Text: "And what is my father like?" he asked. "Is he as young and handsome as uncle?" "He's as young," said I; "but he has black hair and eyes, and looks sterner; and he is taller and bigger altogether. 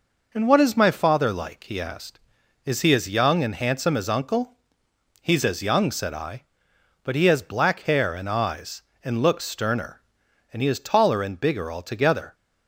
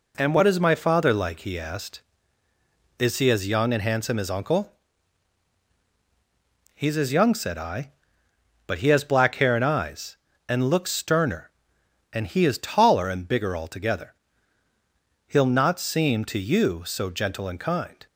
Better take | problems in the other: first | goes on to say "He'll not seem to you so gentle and kind"; strong; from 15.2 s on; 2.7 s long

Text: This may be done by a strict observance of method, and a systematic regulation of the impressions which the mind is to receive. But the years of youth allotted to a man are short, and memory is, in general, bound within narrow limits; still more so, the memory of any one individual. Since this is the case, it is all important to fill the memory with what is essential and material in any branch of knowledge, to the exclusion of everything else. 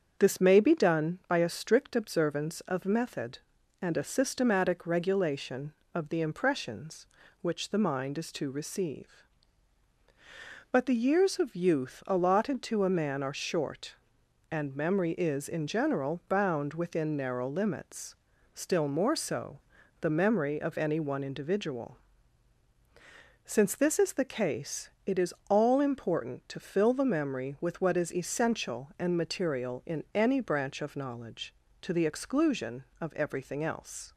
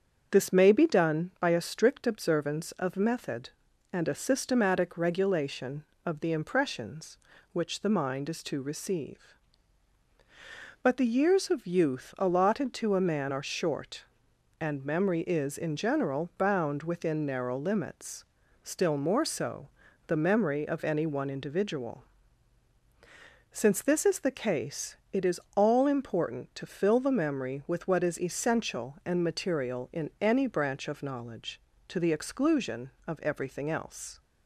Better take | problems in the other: neither | starts louder than the rest; the same in both // pauses between "is" and "all"; slight; the same in both

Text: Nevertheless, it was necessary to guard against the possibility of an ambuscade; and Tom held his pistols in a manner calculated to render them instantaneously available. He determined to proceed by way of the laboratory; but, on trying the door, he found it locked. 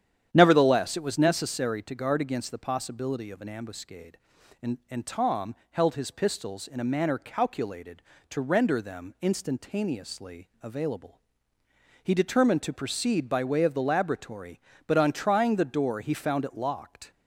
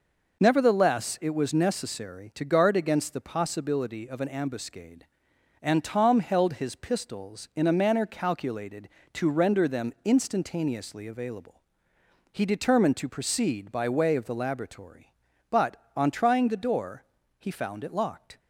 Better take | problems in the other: second | starts louder than the rest; strong; until 1.3 s; 9.5 dB // says "and" twice; at 4.8 s // pauses between "Tom" and "held"; slight; at 5.5 s; 0.16 s long // pauses between "instantaneously" and "available"; slight; at 10.4 s; 0.16 s long

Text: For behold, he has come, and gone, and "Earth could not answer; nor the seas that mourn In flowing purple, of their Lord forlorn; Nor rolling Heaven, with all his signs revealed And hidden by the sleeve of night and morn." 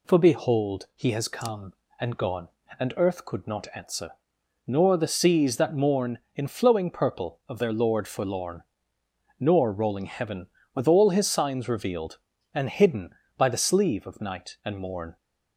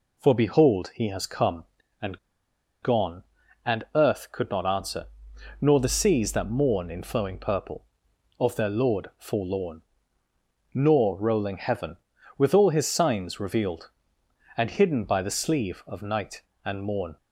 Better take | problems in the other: first | pauses between "and" and "gone"; noticeable; at 2.1 s; 0.65 s long

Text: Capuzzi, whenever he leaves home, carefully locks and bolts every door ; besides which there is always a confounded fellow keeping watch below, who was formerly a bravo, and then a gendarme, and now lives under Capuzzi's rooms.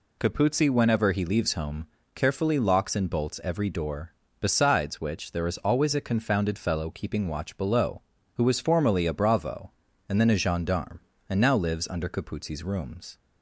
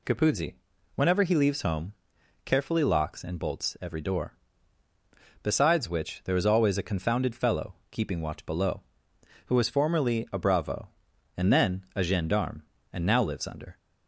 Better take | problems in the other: first | pauses between "fellow" and "keeping"; slight; at 7.7 s; 0.16 s long // stops before "Capuzzi's rooms"; at 13.7 s

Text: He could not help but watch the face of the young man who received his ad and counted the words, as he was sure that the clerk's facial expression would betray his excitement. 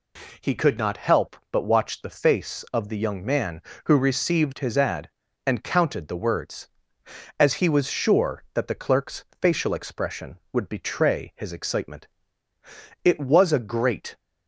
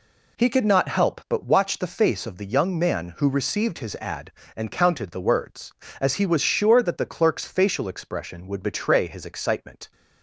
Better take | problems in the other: second | pauses between "clerk's" and "facial"; slight; at 9.2 s; 0.16 s long // goes on to say "It was a great"; noticeable; from 13.0 s on; 1.1 s long

